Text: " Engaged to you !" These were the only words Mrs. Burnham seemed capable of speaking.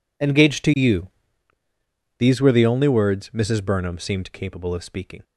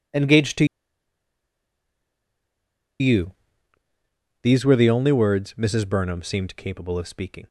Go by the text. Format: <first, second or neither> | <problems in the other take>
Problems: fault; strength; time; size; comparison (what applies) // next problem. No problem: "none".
first | pauses between "to" and "you"; strong; at 0.6 s; 2.3 s long